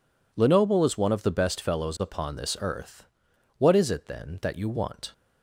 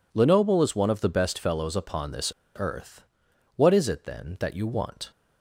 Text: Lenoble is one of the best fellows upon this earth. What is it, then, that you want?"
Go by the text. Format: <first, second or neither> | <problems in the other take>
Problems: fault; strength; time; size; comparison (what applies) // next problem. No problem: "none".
first | pauses between "this" and "earth"; slight; at 2.3 s; 0.26 s long